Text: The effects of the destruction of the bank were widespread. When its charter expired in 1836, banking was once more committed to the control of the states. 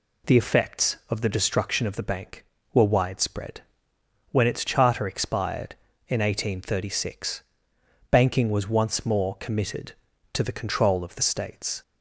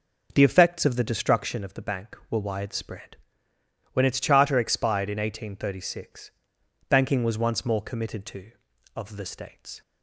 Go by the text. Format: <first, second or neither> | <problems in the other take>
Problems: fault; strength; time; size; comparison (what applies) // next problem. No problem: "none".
first | skips "the control"; at 8.7 s